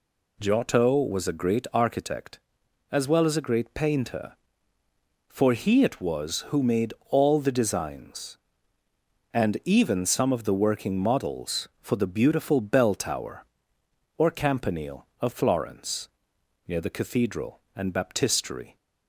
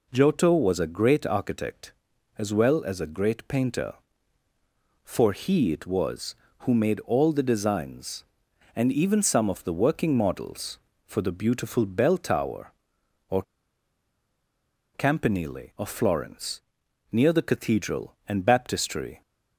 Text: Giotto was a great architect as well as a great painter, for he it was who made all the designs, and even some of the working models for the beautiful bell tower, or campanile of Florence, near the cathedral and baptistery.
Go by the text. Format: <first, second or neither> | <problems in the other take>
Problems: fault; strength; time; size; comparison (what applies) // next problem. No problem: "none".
first | pauses between "or" and "campanile"; strong; at 13.4 s; 1.5 s long